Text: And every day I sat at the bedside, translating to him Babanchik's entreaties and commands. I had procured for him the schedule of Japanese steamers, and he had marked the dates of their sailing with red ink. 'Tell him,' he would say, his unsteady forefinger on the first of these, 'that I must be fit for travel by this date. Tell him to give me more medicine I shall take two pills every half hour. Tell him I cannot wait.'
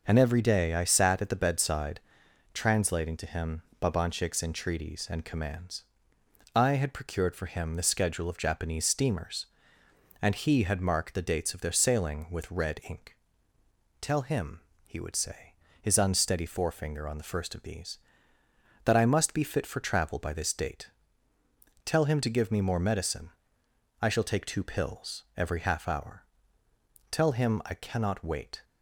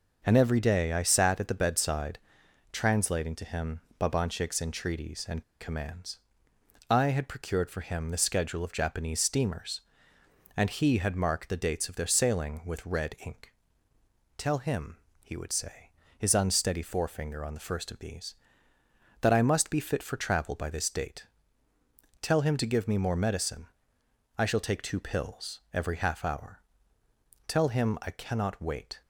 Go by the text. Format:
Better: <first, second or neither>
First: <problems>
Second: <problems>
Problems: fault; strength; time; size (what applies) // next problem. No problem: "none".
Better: first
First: pauses between "him" and "Babanchik's"; slight; at 3.6 s; 0.18 s long // pauses between "medicine" and "I"; noticeable; at 23.3 s; 0.70 s long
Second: pauses between "him" and "Babanchik's"; slight; at 3.8 s; 0.18 s long // pauses between "and" and "commands"; slight; at 5.4 s; 0.17 s long // pauses between "medicine" and "I"; noticeable; at 23.6 s; 0.70 s long